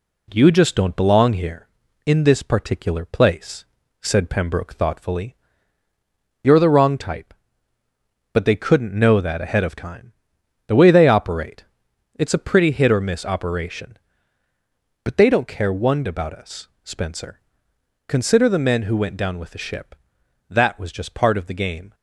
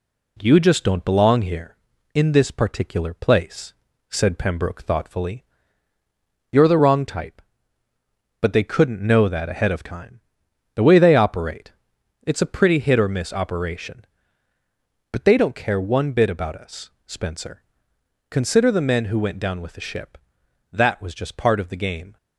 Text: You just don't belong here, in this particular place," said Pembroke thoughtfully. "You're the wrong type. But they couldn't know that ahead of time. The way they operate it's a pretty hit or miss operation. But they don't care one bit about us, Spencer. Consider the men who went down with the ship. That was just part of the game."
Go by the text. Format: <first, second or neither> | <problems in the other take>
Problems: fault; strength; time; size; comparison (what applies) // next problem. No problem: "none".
second | pauses between "operate" and "it's"; noticeable; at 11.6 s; 0.54 s long; noticeable in the second // skips "bit"; at 16.0 s